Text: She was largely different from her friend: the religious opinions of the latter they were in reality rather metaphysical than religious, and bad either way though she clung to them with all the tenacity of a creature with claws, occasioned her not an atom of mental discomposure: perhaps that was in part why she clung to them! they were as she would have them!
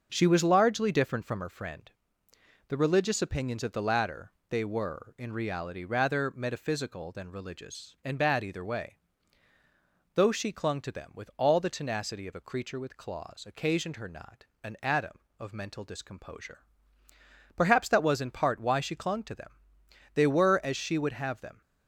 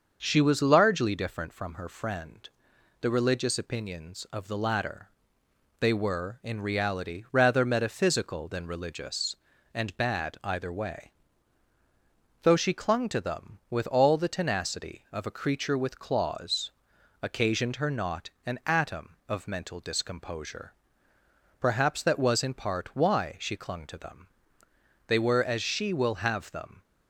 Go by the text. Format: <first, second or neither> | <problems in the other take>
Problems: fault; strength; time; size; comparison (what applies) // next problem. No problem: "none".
first | starts louder than the rest; until 1.2 s; 6.5 dB; also in the first // pauses between "latter" and "they"; noticeable; at 5.0 s; 0.70 s long; slight in the first // pauses between "way" and "though"; strong; at 11.0 s; 1.3 s long; also in the first // pauses between "not" and "an"; slight; at 18.2 s; 0.16 s long; slight in the first // says "will" for "would"; at 25.9 s